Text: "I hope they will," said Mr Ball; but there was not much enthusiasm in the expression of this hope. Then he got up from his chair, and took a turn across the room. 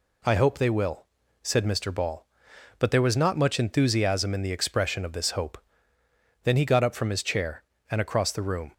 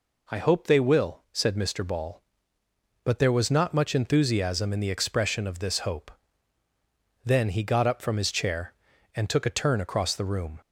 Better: second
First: skips "took a turn"; at 7.9 s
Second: none

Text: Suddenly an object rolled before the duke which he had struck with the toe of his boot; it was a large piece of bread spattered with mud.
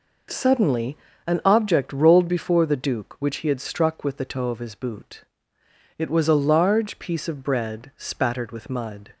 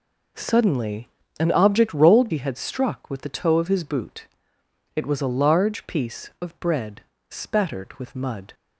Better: first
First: pauses between "Suddenly" and "an"; slight; at 0.9 s; 0.30 s long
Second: pauses between "Suddenly" and "an"; slight; at 1.0 s; 0.32 s long // skips "before the duke which"; at 2.2 s // pauses between "bread" and "spattered"; slight; at 7.0 s; 0.28 s long

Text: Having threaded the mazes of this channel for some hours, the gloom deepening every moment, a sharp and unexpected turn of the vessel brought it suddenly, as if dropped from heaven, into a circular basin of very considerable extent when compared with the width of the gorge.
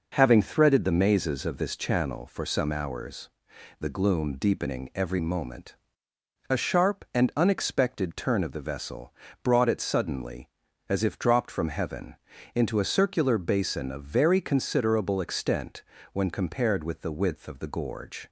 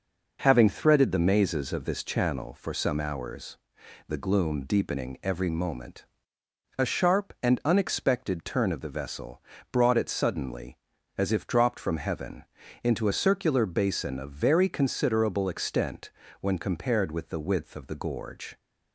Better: neither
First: pauses between "vessel" and "brought"; slight; at 9.1 s; 0.32 s long // pauses between "extent" and "when"; slight; at 15.8 s; 0.28 s long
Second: pauses between "vessel" and "brought"; slight; at 9.4 s; 0.32 s long // pauses between "extent" and "when"; slight; at 16.1 s; 0.28 s long

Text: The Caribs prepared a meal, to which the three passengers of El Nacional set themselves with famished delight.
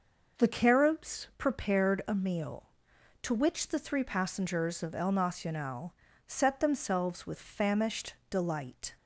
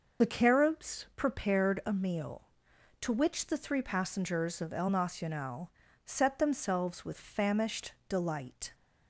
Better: first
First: pauses between "Nacional" and "set"; slight; at 5.9 s; 0.32 s long // pauses between "famished" and "delight"; slight; at 8.1 s; 0.16 s long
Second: loses the start of "The"; at 0.2 s; 40 ms // pauses between "Nacional" and "set"; slight; at 5.7 s; 0.34 s long // pauses between "famished" and "delight"; slight; at 7.9 s; 0.16 s long

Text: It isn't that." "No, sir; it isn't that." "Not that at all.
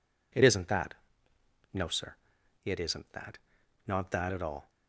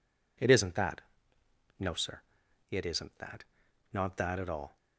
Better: neither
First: none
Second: none

